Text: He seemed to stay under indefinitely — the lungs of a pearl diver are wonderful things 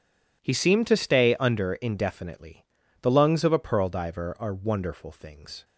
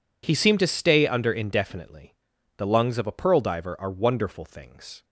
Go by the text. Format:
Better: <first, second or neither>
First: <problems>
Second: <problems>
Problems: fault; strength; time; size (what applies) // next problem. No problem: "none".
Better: neither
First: none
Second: none